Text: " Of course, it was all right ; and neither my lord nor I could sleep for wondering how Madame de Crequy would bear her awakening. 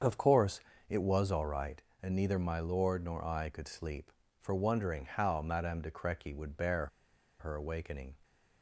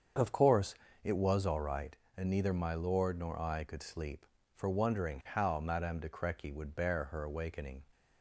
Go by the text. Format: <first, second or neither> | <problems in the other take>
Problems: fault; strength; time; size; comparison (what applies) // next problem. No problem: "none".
second | starts louder than the rest; until 1.3 s; 7 dB; also in the second // pauses between "bear" and "her"; noticeable; at 6.8 s; 0.53 s long